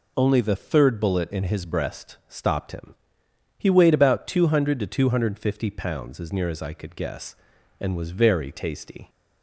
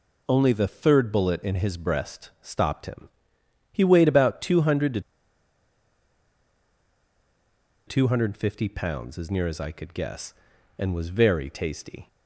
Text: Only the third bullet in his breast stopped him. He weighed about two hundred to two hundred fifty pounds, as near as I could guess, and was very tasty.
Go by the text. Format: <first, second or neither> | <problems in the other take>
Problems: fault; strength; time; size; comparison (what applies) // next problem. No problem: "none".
first | pauses between "to" and "two"; strong; at 5.0 s; 2.8 s long